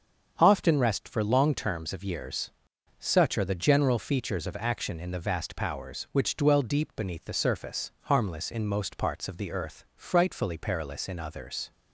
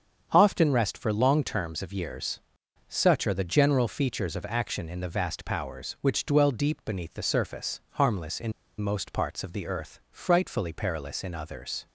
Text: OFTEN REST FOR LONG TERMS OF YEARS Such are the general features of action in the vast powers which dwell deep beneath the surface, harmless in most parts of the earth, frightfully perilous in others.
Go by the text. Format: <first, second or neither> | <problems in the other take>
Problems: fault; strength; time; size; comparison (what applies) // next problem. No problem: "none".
first | starts louder than the rest; strong; until 1.3 s; 7 dB; strong in the first // pauses between "YEARS" and "Such"; noticeable; at 2.3 s; 0.48 s long; noticeable in the first // pauses between "in" and "most"; slight; at 8.5 s; 0.28 s long